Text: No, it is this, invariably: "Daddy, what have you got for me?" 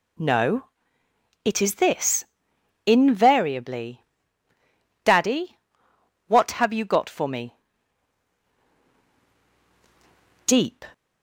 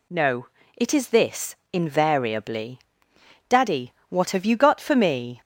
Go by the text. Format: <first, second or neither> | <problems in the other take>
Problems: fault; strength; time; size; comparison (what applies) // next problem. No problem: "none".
second | goes on to say "Deep"; slight; from 10.4 s on; 0.40 s long